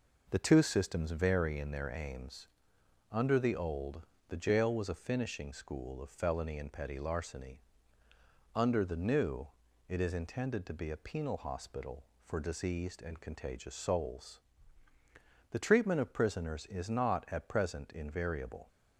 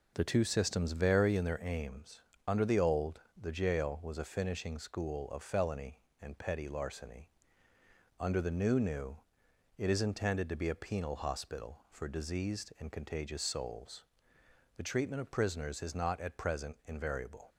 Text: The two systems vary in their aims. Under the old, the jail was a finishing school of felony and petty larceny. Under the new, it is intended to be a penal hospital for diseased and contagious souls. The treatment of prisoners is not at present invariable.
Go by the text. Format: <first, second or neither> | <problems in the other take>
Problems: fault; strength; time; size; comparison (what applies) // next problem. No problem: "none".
first | says "new" twice; at 8.7 s